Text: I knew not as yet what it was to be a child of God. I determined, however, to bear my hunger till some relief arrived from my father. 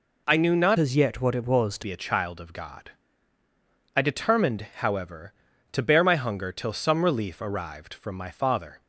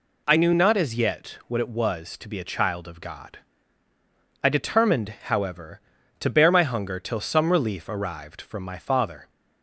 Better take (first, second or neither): second